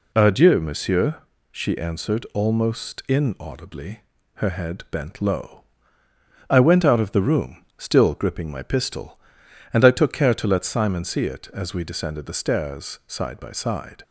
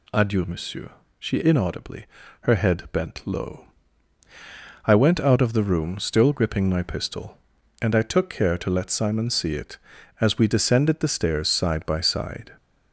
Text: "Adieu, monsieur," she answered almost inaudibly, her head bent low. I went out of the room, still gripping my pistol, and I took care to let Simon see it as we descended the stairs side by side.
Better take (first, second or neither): first